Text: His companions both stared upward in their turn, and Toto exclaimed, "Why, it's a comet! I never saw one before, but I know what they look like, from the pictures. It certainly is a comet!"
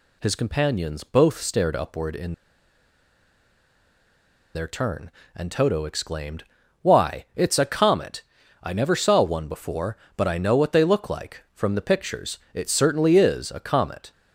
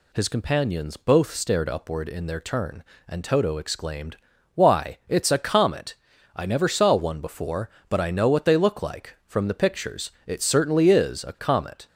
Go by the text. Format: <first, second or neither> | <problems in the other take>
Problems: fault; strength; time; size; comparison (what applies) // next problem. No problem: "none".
second | pauses between "in" and "their"; strong; at 2.3 s; 2.2 s long